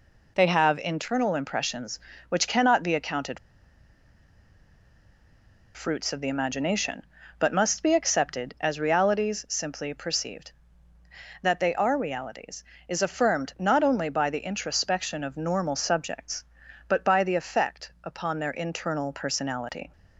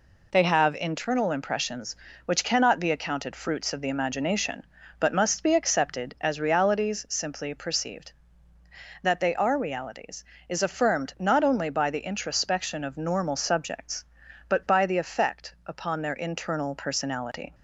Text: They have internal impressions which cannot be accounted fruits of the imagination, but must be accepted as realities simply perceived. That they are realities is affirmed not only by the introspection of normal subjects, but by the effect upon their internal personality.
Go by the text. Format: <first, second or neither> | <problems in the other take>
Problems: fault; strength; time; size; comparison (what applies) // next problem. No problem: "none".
second | pauses between "accounted" and "fruits"; strong; at 3.3 s; 2.3 s long